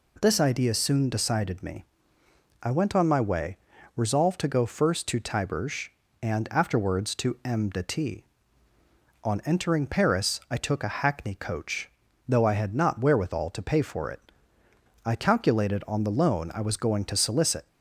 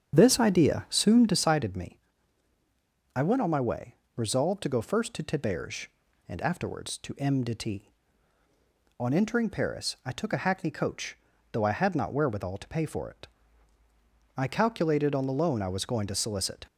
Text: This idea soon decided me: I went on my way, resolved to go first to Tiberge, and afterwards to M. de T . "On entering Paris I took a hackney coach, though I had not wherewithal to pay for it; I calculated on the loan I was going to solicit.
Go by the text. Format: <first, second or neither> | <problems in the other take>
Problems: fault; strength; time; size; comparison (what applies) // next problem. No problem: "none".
first | starts louder than the rest; strong; until 1.4 s; 8.5 dB